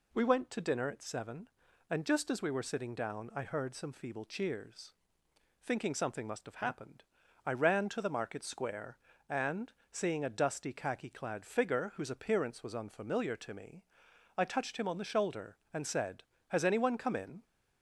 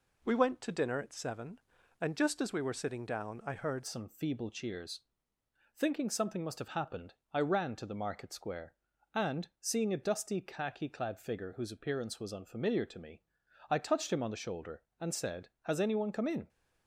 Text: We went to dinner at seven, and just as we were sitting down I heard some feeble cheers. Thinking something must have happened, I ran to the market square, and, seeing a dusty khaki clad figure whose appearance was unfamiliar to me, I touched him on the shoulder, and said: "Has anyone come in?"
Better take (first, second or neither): first